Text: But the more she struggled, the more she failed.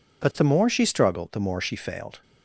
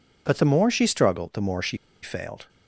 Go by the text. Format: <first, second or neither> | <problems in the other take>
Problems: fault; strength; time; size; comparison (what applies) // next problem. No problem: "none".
first | pauses between "she" and "failed"; slight; at 1.7 s; 0.25 s long